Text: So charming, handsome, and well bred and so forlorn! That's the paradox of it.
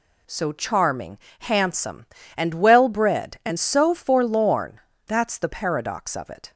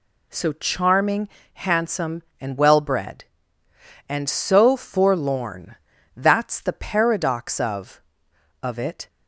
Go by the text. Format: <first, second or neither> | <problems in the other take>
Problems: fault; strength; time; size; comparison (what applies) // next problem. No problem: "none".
first | says "of" twice; at 8.6 s